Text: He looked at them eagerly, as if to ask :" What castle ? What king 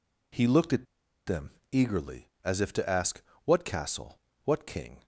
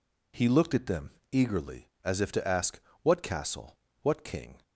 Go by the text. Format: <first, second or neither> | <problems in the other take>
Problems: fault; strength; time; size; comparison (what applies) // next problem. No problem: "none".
second | pauses between "at" and "them"; at 0.8 s; 0.41 s long // pauses between "them" and "eagerly"; slight; at 1.5 s; 0.20 s long; slight in the second